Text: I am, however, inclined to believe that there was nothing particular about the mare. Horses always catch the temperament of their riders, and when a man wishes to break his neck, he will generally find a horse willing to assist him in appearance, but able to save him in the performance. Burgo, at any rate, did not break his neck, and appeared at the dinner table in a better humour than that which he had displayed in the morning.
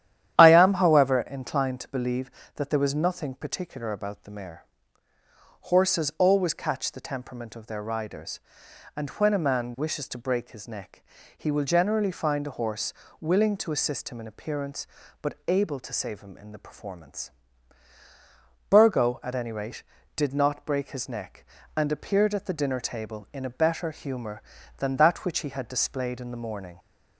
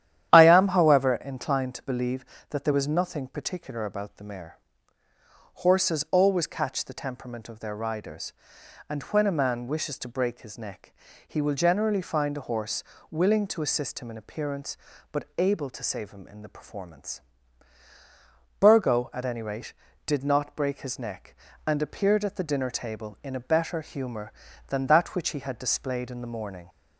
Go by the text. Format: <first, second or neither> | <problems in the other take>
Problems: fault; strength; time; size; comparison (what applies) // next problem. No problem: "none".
neither | starts louder than the rest; strong; the same in both // pauses between "horse" and "willing"; slight; the same in both